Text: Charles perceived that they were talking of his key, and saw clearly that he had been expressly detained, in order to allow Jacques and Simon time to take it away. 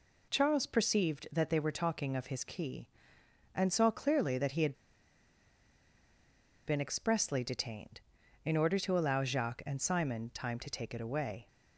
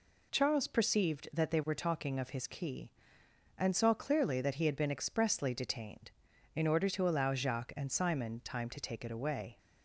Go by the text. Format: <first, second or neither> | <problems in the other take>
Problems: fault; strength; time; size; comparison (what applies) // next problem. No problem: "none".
second | pauses between "had" and "been"; strong; at 4.7 s; 1.9 s long